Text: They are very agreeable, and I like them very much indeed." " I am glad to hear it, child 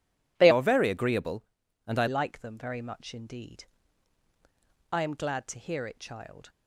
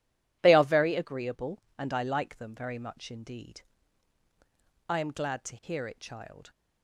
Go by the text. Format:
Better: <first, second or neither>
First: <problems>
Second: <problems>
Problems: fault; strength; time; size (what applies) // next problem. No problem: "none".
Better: second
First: starts louder than the rest; strong; until 1.3 s; 12 dB // changes voice from "are" to "I"; from 0.5 to 2.0 s; 1.5 s long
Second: starts louder than the rest; strong; until 1.4 s; 13.5 dB